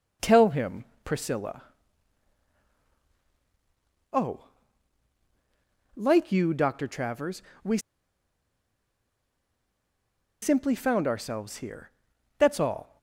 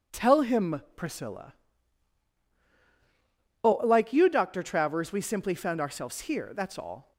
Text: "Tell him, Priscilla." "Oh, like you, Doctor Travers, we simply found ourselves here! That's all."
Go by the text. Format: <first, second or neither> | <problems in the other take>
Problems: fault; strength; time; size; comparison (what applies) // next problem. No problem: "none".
second | pauses between "we" and "simply"; strong; at 7.7 s; 2.6 s long